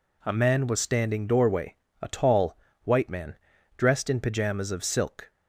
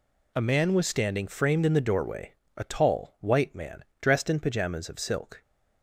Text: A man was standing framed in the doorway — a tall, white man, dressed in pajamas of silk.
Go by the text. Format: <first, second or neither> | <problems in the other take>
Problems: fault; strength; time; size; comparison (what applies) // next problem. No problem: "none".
second | skips "framed in the"; at 1.2 s